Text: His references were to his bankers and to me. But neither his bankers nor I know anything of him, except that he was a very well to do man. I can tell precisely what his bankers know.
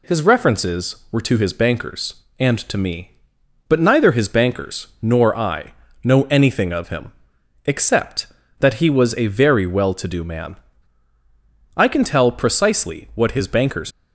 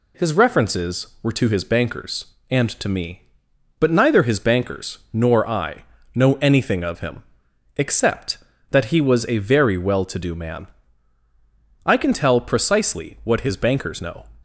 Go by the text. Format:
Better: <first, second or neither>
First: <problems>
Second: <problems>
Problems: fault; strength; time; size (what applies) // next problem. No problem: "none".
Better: second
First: pauses between "I" and "know"; slight; at 5.7 s; 0.30 s long // stops before "know"; at 13.9 s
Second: pauses between "I" and "know"; slight; at 5.8 s; 0.30 s long